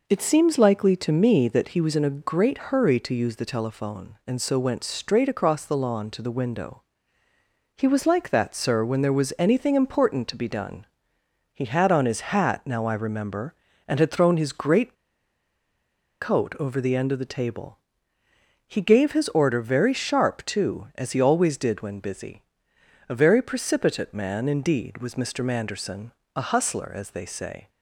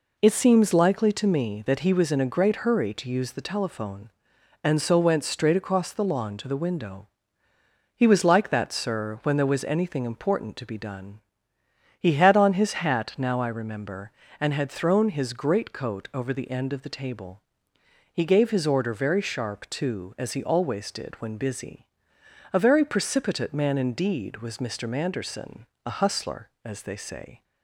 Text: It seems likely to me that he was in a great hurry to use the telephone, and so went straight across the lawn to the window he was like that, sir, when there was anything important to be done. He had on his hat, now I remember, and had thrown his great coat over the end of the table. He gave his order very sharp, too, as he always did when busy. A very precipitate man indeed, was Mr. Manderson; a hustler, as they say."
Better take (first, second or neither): second